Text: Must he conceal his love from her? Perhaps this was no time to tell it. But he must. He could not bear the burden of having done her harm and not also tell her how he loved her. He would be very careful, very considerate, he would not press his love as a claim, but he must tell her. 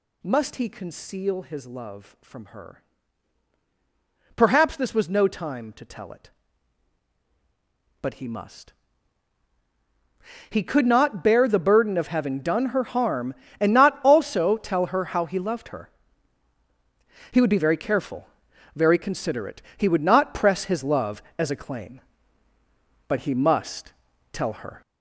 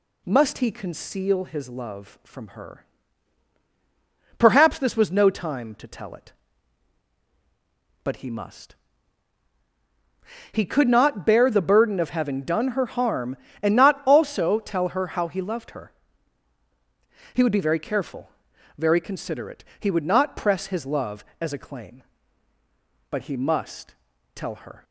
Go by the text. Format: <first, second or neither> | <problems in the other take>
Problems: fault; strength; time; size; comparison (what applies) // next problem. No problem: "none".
second | gets louder; throughout; 6.5 dB // pauses between "must" and "tell"; at 23.9 s; 0.38 s long; also in the second